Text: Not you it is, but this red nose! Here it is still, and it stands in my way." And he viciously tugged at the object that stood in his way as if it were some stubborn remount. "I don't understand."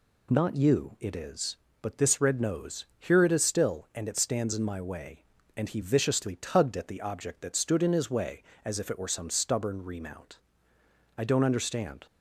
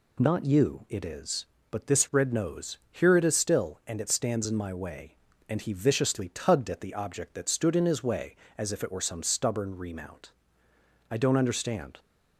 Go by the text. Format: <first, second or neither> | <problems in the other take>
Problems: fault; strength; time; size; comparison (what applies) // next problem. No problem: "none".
neither | none